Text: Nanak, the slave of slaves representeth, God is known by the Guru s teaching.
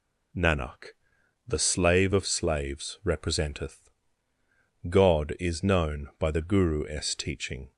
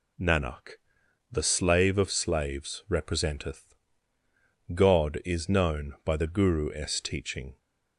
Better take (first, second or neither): neither